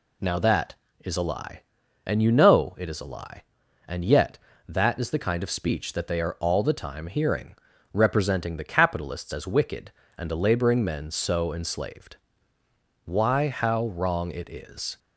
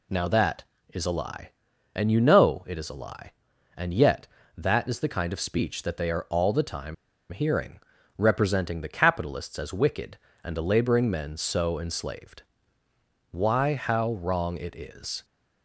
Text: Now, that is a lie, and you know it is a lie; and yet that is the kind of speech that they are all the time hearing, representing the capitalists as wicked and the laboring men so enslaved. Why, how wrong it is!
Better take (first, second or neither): first